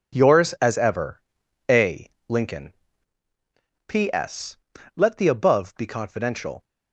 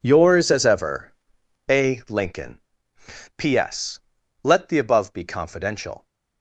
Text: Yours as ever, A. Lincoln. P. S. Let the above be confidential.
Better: neither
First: none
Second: none

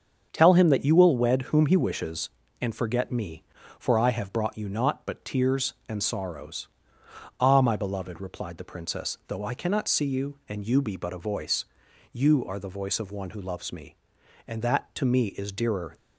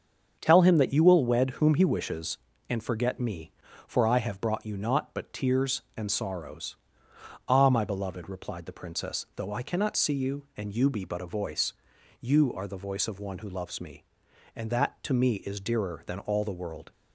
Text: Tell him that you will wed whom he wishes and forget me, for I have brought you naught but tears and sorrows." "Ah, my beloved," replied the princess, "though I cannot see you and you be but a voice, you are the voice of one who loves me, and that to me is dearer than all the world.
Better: second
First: starts louder than the rest; until 1.3 s; 7 dB // stops before "than all the world"; at 15.9 s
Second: starts louder than the rest; until 1.4 s; 7 dB

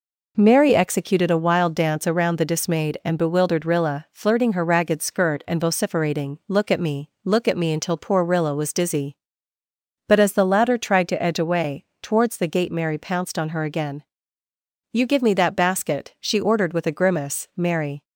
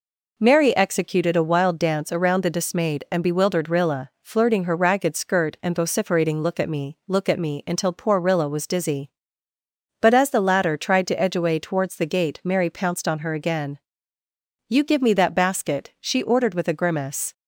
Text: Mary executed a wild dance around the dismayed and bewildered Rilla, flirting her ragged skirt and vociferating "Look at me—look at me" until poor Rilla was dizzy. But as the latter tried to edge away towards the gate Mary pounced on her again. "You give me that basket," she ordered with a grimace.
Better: second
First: pauses between "away" and "towards"; slight; at 11.8 s; 0.16 s long // goes on to say "Mary"; slight; from 17.5 s on; 0.48 s long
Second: none

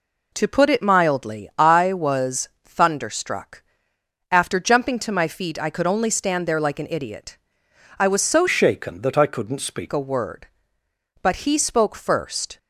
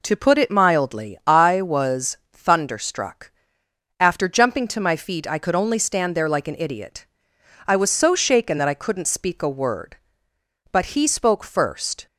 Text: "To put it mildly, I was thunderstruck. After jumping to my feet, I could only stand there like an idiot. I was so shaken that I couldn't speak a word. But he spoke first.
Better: second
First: pauses between "was" and "thunderstruck"; slight; at 2.4 s; 0.16 s long // changes voice from "shaken" to "speak"; from 8.4 to 9.8 s; 1.4 s long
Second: pauses between "was" and "thunderstruck"; slight; at 2.1 s; 0.16 s long

